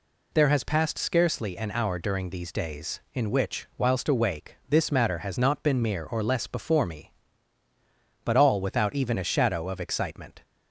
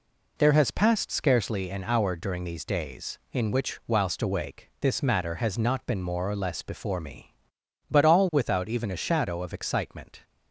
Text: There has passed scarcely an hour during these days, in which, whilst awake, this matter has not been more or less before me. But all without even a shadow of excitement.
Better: second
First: says "mere" for "more"; at 5.8 s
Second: none

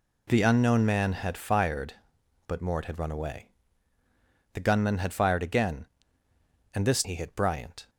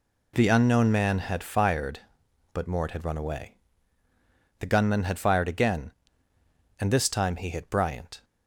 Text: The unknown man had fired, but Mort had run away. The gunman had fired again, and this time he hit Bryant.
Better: second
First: skips "time"; at 7.0 s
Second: none

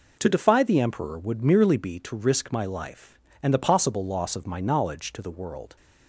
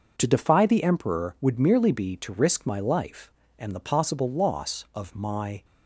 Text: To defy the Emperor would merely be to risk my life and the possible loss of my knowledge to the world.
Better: first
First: none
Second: stops before "knowledge to the world"; at 5.6 s

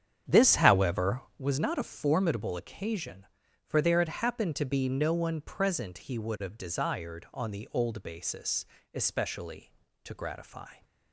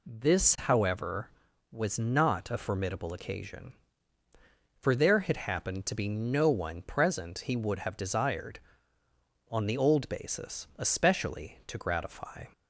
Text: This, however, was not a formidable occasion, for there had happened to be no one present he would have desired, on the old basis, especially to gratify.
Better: second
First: starts louder than the rest; strong; until 1.3 s; 8.5 dB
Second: none

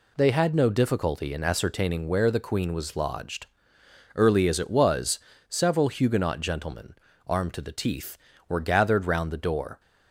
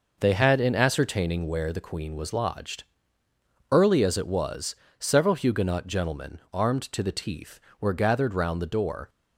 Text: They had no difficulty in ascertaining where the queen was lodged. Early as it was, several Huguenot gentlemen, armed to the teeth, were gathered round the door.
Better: first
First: none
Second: skips "no difficulty"; at 0.5 s

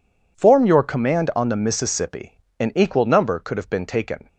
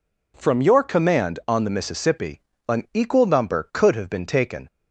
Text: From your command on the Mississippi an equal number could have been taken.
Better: second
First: says "Form" for "From"; at 0.3 s // pauses between "Mississippi" and "an"; slight; at 2.3 s; 0.22 s long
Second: pauses between "Mississippi" and "an"; slight; at 2.4 s; 0.26 s long

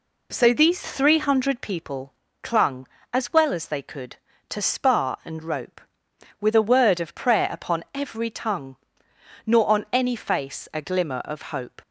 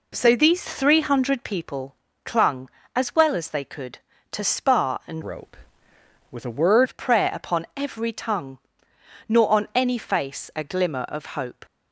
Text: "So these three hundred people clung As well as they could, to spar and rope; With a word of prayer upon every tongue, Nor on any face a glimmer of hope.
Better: first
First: pauses between "people" and "clung"; slight; at 2.1 s; 0.28 s long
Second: pauses between "people" and "clung"; slight; at 1.9 s; 0.28 s long // changes voice from "rope" to "word"; from 5.2 to 6.8 s; 1.6 s long

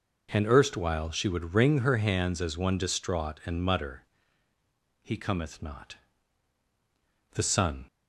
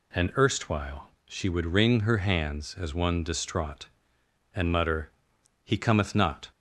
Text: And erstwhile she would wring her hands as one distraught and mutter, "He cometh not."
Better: second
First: goes on to say "The sun"; from 7.3 s on; 0.54 s long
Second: none

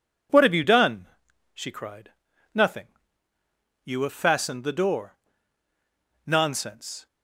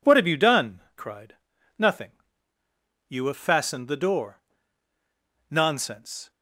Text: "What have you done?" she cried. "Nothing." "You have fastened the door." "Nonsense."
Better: first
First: none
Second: skips "she"; at 0.8 s

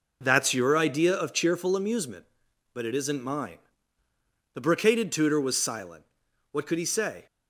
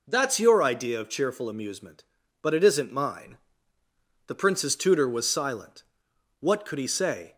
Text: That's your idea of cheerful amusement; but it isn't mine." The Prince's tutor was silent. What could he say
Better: second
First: says "Brocaded" for "Prince's"; at 4.5 s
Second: none

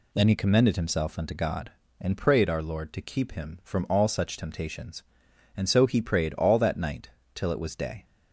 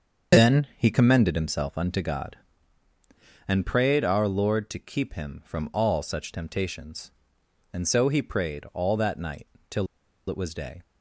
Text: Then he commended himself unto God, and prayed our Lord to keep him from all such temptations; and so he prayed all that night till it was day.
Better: first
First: pauses between "night" and "till"; slight; at 7.0 s; 0.25 s long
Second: starts louder than the rest; until 1.4 s; 6 dB // pauses between "night" and "till"; slight; at 9.4 s; 0.24 s long // pauses between "till" and "it"; at 9.8 s; 0.42 s long

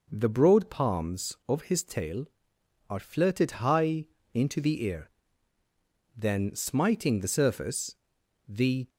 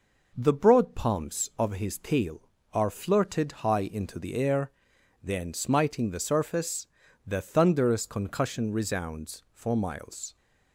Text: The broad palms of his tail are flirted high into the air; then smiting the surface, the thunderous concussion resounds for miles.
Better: second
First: pauses between "high" and "into"; slight; at 4.0 s; 0.28 s long // stops before "thunderous concussion resounds for miles"; at 8.8 s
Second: none

